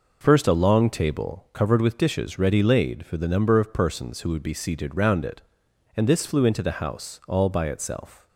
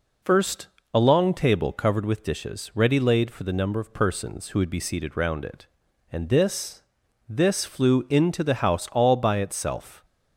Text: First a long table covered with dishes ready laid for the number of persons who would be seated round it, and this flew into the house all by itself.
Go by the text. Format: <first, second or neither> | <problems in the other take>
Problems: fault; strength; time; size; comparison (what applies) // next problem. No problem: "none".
first | pauses between "First" and "a"; slight; at 0.6 s; 0.26 s long // says "this" twice; at 7.2 s